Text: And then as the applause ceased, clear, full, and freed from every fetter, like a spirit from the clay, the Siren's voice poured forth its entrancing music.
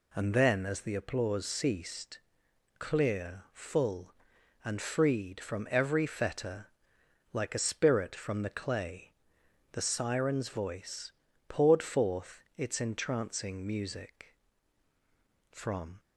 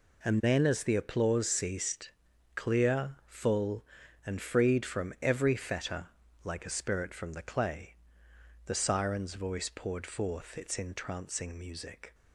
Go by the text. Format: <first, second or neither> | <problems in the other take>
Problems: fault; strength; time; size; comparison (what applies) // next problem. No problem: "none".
second | pauses between "voice" and "poured"; slight; at 11.1 s; 0.36 s long // pauses between "forth" and "its"; slight; at 12.4 s; 0.16 s long // goes on to say "From"; slight; from 15.5 s on; 0.48 s long